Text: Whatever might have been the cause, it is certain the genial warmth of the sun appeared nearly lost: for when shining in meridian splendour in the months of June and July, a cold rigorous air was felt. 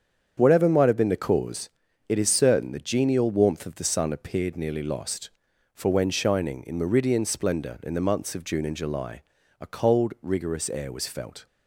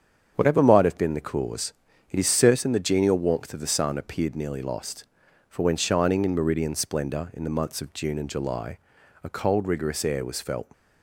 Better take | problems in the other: neither | starts louder than the rest; strong; the same in both

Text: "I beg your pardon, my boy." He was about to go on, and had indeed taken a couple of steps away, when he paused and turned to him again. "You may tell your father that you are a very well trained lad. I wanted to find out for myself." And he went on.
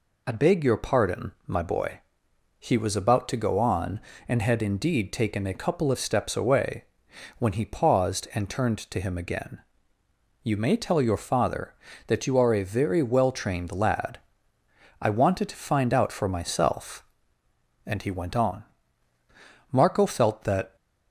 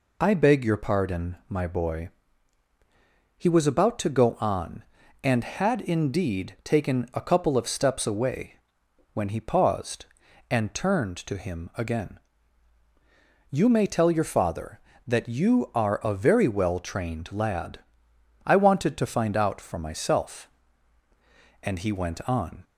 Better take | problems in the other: second | goes on to say "Marco felt that"; noticeable; from 19.7 s on; 1.0 s long

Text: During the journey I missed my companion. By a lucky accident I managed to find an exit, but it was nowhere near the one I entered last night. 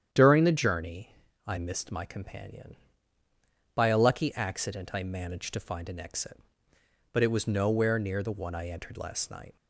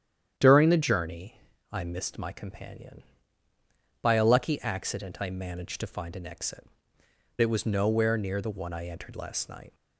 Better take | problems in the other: first | starts louder than the rest; strong; until 1.3 s; 9.5 dB; strong in the first // pauses between "journey" and "I"; slight; at 1.4 s; 0.30 s long; slight in the first // skips "but"; at 7.0 s

